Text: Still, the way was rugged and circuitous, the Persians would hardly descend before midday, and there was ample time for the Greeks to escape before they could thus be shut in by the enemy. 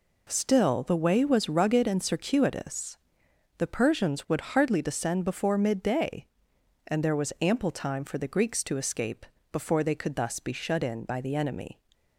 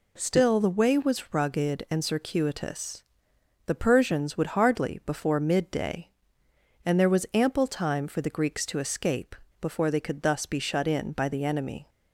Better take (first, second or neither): first